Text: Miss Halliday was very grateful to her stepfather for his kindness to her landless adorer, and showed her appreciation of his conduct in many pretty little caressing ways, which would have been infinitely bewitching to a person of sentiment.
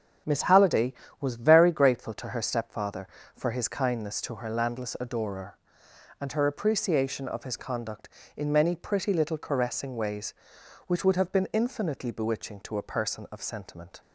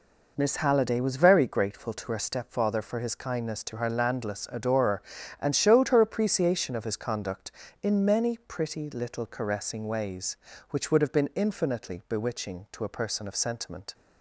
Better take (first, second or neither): second